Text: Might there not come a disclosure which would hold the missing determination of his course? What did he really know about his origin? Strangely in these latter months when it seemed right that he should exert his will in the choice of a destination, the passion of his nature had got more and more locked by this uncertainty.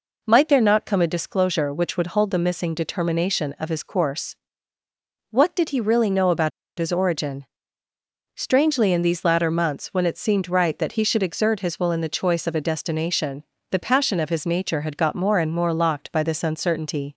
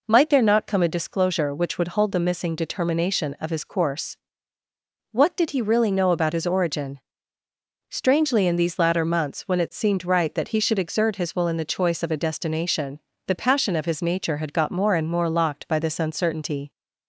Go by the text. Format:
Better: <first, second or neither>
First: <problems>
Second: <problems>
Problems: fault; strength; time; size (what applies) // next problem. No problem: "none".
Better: second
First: pauses between "about" and "his"; slight; at 6.5 s; 0.28 s long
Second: none